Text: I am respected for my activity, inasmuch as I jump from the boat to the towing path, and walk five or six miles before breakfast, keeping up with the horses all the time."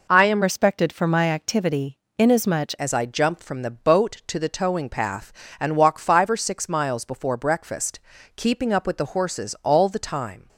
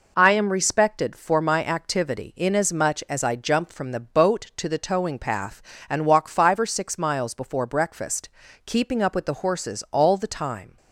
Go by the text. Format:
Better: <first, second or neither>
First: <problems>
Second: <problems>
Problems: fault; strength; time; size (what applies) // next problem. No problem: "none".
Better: second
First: changes voice from "respected" to "inasmuch"; from 0.4 to 2.7 s; 2.3 s long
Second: none